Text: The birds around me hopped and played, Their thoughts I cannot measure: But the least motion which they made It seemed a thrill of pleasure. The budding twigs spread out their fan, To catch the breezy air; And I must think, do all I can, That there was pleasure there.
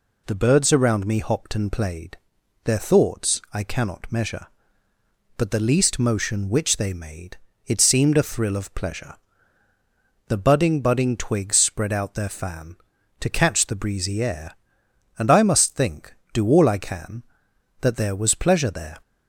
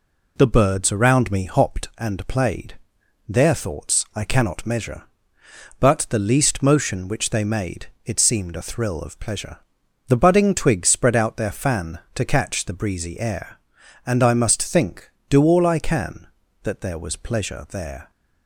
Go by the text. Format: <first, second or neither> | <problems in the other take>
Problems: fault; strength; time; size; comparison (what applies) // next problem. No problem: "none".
second | pauses between "made" and "It"; slight; at 7.3 s; 0.30 s long; slight in the second // says "budding" twice; at 10.7 s